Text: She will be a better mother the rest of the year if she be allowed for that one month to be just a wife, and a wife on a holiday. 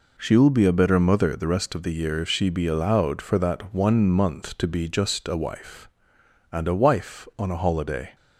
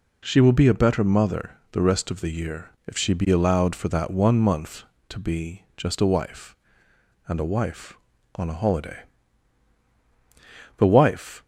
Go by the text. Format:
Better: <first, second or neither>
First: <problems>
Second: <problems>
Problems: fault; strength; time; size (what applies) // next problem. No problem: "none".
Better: first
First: none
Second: pauses between "year" and "if"; slight; at 2.6 s; 0.18 s long // goes on to say "The wife"; noticeable; from 10.7 s on; 0.64 s long